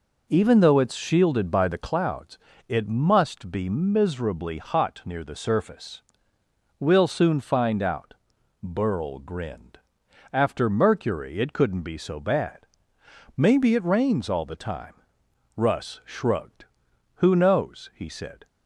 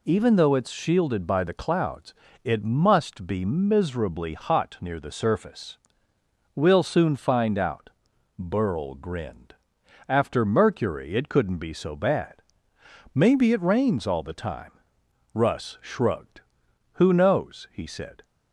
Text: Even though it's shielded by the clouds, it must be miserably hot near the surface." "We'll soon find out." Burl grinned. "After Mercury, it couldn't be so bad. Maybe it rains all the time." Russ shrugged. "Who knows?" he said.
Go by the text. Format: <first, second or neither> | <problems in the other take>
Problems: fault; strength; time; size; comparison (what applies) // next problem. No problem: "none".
second | starts louder than the rest; noticeable; until 1.9 s; 4.5 dB